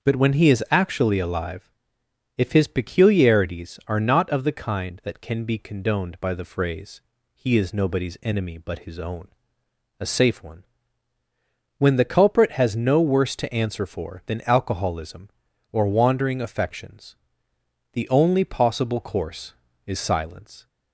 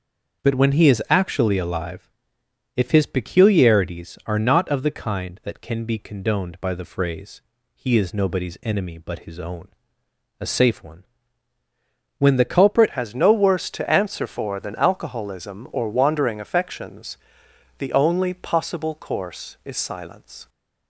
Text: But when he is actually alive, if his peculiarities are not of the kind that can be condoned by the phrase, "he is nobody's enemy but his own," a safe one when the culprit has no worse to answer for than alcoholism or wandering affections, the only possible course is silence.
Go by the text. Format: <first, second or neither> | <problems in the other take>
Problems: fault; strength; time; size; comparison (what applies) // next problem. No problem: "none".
first | starts louder than the rest; until 1.4 s; 6.5 dB; also in the first // pauses between "one" and "when"; at 11.0 s; 1.1 s long; also in the first // changes voice at "has"; from 12.9 s on; 7.5 s long